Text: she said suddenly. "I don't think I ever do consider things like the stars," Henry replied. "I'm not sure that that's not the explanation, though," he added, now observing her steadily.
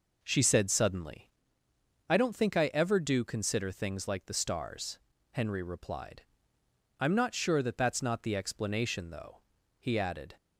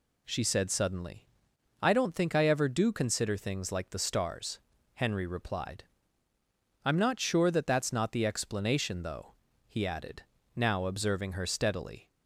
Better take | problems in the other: second | stops before "now observing her steadily"; at 10.3 s

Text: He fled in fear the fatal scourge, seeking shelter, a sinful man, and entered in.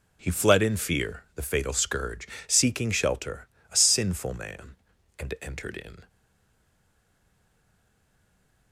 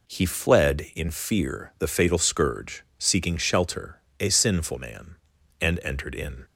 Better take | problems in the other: second | stays silent after the last word; strong; from 6.0 s on; 2.7 s long

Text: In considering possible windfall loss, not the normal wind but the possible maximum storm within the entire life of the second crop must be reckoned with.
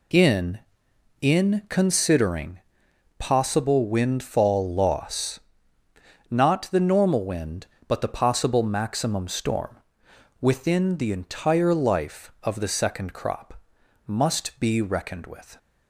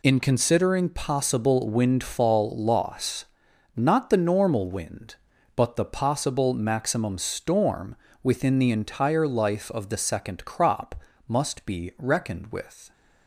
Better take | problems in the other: second | says "In" twice; at 1.2 s // pauses between "considering" and "possible"; noticeable; at 2.5 s; 0.58 s long // pauses between "storm" and "within"; noticeable; at 9.7 s; 0.64 s long; slight in the second // pauses between "crop" and "must"; noticeable; at 13.5 s; 0.52 s long; slight in the second

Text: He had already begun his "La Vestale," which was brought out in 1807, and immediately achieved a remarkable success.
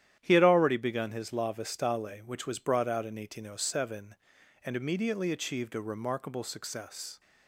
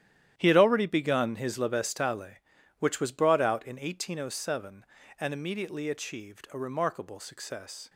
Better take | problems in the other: first | gets quieter; strong; throughout; 13 dB // starts louder than the rest; strong; until 1.3 s; 11 dB; strong in the first

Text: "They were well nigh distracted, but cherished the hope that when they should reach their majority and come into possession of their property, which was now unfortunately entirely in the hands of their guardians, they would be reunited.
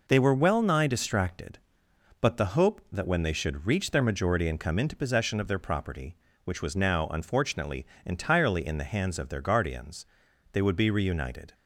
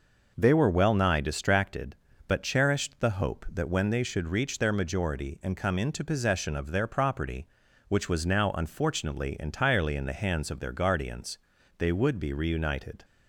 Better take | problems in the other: second | skips "cherished"; at 2.3 s // pauses between "unfortunately" and "entirely"; slight; at 7.8 s; 0.20 s long

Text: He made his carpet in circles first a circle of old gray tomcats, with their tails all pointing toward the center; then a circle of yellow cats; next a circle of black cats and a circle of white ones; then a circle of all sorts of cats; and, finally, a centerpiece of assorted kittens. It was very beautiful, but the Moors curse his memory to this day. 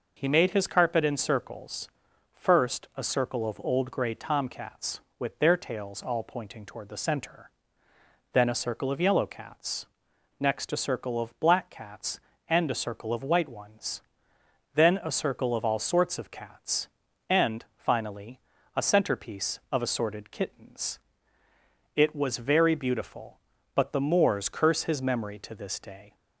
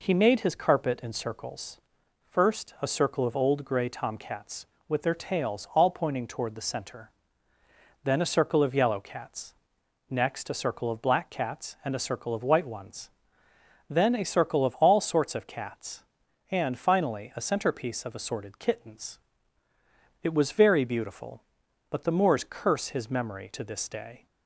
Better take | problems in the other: neither | pauses between "circles" and "first"; the same in both

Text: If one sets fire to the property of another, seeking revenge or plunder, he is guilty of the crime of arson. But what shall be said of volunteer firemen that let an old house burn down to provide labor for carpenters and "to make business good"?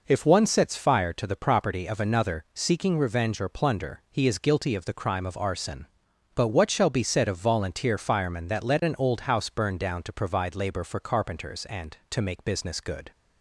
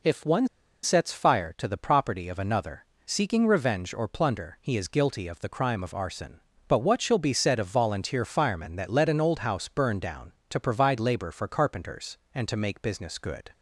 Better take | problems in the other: first | pauses between "one" and "sets"; slight; at 0.4 s; 0.35 s long

